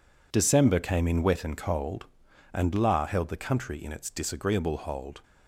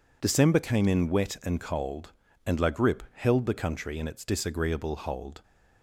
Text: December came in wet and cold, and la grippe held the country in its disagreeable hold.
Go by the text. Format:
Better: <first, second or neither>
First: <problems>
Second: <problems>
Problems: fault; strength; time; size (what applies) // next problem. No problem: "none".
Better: second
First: skips "grippe"; at 3.0 s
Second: none